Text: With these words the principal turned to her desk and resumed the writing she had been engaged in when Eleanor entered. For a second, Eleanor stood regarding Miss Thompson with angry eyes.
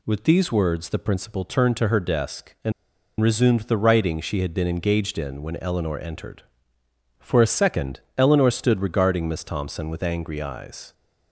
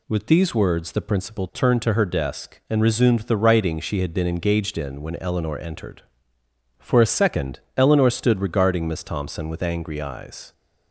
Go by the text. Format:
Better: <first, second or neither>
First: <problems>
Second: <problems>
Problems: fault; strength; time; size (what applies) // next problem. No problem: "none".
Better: second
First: pauses between "and" and "resumed"; noticeable; at 2.7 s; 0.48 s long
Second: none